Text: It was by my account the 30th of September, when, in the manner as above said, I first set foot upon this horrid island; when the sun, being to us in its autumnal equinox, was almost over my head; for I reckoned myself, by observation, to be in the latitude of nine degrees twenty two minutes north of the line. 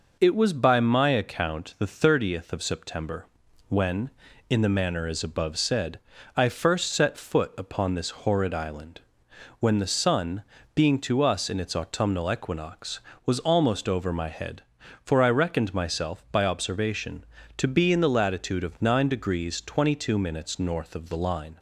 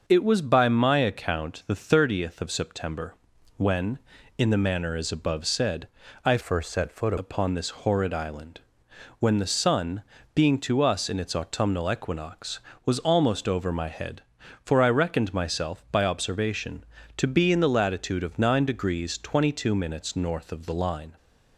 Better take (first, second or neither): first